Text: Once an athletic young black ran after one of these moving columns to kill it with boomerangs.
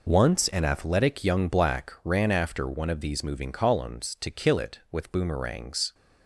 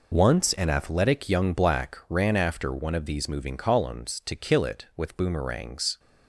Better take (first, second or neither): neither